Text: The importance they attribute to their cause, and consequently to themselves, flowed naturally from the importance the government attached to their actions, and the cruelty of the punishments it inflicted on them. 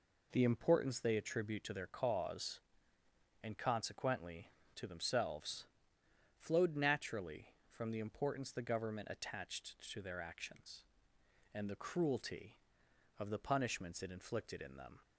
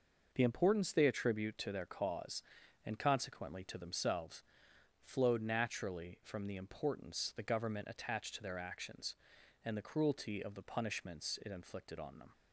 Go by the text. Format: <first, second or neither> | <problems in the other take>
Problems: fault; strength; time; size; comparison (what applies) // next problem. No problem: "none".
second | says "in" for "on"; at 14.6 s